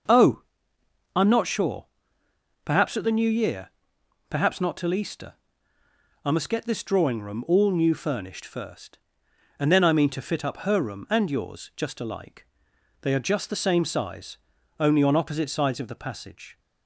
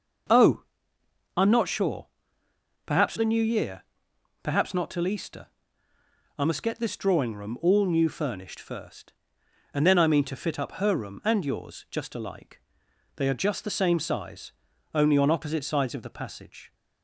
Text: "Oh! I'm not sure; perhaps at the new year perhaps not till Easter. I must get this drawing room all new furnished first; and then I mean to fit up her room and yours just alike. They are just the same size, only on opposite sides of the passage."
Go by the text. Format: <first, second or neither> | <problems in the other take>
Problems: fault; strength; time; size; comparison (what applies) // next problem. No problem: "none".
first | skips "at"; at 3.1 s // pauses between "year" and "perhaps"; noticeable; at 3.8 s; 0.58 s long; noticeable in the first